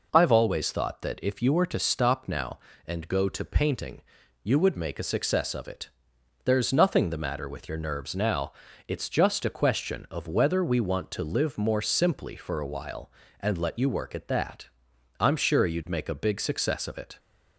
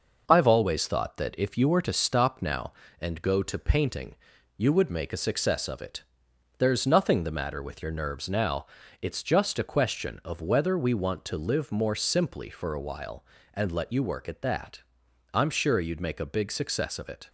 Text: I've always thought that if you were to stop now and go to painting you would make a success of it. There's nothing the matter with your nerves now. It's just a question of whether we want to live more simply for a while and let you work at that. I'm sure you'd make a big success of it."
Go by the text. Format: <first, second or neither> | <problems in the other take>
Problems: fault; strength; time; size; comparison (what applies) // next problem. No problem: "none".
first | gets quieter; noticeable; throughout; 4.5 dB // pauses between "painting" and "you"; at 4.1 s; 0.40 s long; also in the first